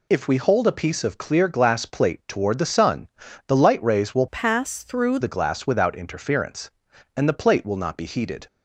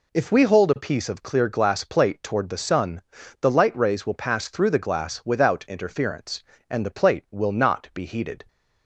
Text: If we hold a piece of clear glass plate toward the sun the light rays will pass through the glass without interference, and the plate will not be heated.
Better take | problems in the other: second | pauses between "sun" and "the"; at 3.0 s; 0.40 s long; also in the second // changes voice from "pass" to "through"; from 4.2 to 5.1 s; 0.9 s long

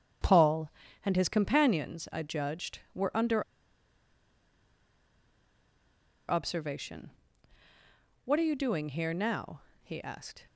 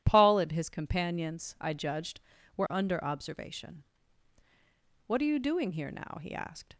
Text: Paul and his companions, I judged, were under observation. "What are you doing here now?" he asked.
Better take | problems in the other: second | starts louder than the rest; strong; until 1.5 s; 8.5 dB // pauses between "under" and "observation"; strong; at 3.4 s; 2.8 s long

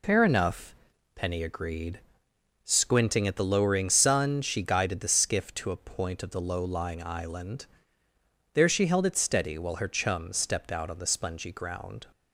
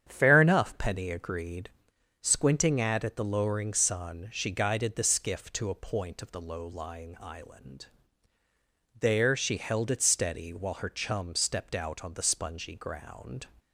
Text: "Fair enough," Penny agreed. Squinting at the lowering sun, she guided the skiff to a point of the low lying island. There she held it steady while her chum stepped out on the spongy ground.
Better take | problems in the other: first | starts louder than the rest; strong; until 1.1 s; 8.5 dB // says "at" twice; at 3.0 s

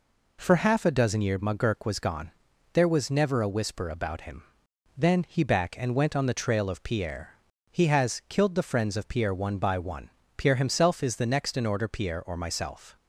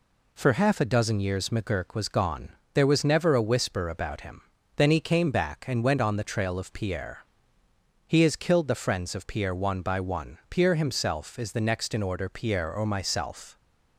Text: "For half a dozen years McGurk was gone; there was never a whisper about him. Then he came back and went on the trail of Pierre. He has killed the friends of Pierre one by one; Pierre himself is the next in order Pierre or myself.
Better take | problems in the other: second | skips "came"; at 5.4 s

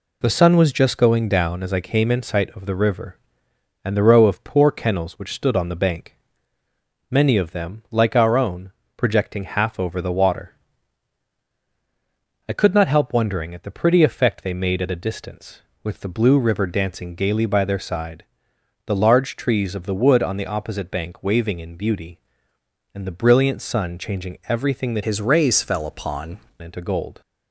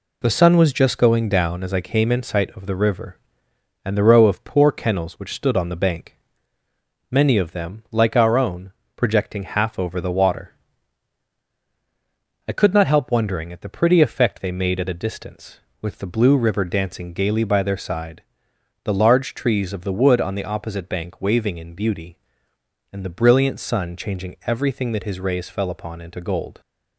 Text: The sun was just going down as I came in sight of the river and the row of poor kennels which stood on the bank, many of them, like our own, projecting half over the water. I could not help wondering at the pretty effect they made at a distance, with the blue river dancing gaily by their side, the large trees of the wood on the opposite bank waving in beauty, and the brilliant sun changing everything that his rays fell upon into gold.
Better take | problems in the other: second | changes voice from "his" to "upon"; from 25.0 to 26.3 s; 1.3 s long

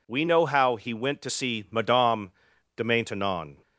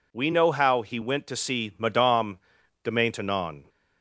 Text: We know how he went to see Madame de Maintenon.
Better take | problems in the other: neither | pauses between "Madame" and "de"; noticeable; the same in both

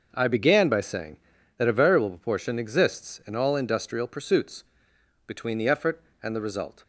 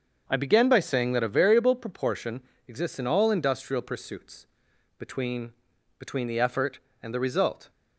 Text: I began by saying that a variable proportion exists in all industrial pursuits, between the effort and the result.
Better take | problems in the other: first | starts louder than the rest; until 1.2 s; 6.5 dB // pauses between "proportion" and "exists"; slight; at 2.4 s; 0.24 s long // says "between" twice; at 5.9 s

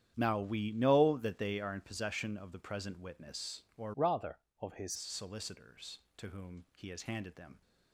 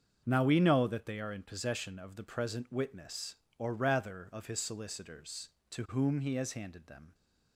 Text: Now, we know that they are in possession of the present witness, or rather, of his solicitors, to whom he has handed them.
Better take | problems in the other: second | starts louder than the rest; strong; until 1.1 s; 10 dB; also in the second // changes voice from "rather" to "his"; from 3.9 to 4.9 s; 1.0 s long

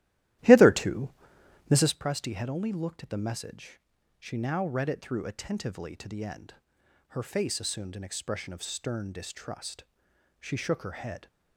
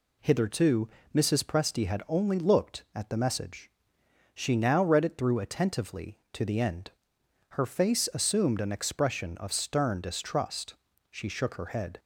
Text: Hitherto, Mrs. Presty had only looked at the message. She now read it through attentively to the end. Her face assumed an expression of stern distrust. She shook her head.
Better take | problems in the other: second | starts louder than the rest; strong; until 2.0 s; 14.5 dB

